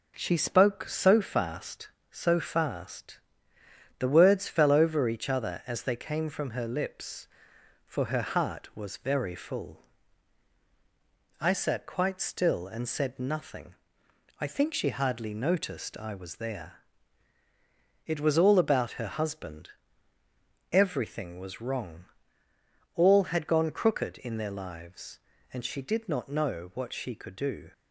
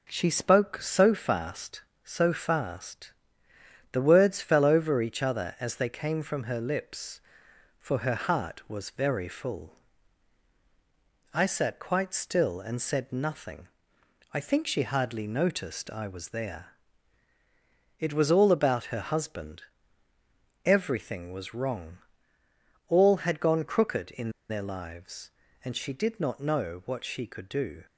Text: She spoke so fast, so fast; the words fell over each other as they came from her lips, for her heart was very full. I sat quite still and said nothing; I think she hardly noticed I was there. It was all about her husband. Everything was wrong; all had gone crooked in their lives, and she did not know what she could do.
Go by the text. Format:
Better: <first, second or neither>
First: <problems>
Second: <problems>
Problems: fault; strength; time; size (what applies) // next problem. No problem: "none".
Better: first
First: none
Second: pauses between "in" and "their"; slight; at 24.2 s; 0.19 s long